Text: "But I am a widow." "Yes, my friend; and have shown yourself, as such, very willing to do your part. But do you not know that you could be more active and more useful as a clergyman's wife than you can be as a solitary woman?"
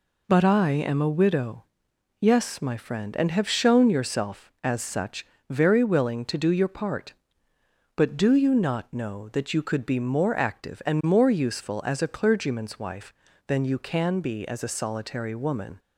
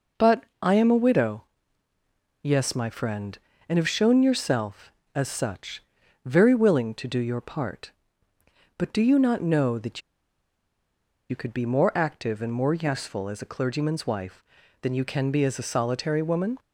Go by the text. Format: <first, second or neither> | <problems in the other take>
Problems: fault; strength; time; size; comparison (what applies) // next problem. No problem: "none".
first | pauses between "But" and "I"; slight; at 0.4 s; 0.18 s long // pauses between "that" and "you"; strong; at 10.0 s; 1.2 s long